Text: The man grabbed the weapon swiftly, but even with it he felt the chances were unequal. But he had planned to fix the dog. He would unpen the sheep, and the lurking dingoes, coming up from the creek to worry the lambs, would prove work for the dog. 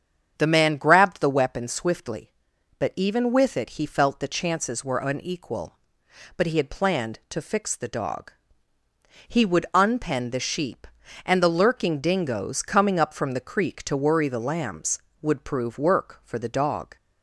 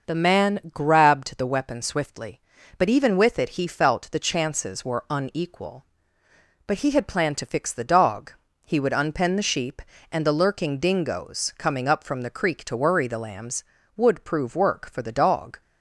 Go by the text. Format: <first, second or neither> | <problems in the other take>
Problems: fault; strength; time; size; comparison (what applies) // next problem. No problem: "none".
neither | starts louder than the rest; the same in both